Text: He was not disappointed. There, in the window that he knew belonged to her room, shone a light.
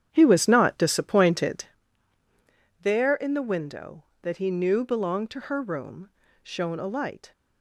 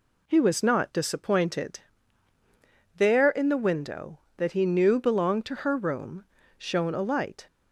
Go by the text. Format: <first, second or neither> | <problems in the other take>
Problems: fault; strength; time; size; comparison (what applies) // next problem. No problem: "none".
second | starts louder than the rest; strong; until 1.8 s; 9 dB